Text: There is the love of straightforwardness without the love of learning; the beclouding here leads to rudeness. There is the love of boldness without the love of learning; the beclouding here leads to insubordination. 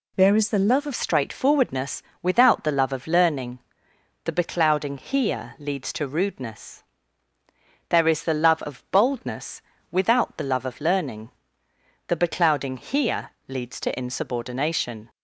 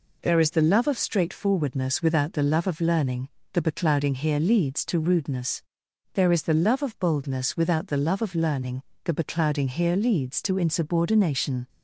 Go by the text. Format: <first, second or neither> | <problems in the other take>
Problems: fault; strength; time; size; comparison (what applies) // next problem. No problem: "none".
second | changes voice at "straightforwardness"; from 0.9 s on; 14.1 s long // pauses between "straightforwardness" and "without"; slight; at 2.0 s; 0.20 s long // pauses between "boldness" and "without"; slight; at 9.5 s; 0.30 s long // pauses between "here" and "leads"; slight; at 13.3 s; 0.16 s long